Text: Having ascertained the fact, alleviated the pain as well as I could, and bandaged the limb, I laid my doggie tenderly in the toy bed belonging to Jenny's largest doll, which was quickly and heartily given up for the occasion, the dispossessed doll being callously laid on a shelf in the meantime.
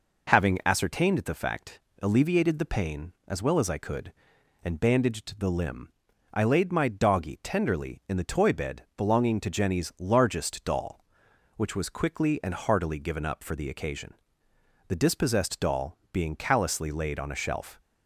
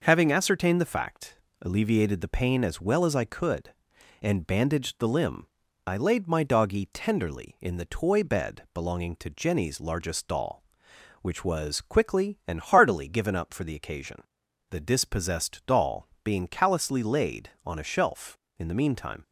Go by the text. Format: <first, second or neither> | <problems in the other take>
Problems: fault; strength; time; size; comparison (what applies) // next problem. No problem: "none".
second | pauses between "bed" and "belonging"; slight; at 8.8 s; 0.16 s long // pauses between "doll" and "being"; slight; at 15.9 s; 0.16 s long; slight in the second // stops before "in the meantime"; at 17.8 s